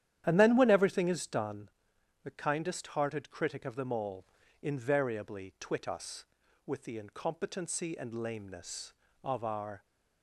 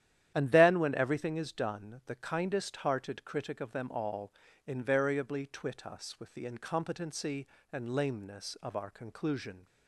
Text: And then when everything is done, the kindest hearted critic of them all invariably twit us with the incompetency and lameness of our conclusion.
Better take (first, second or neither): second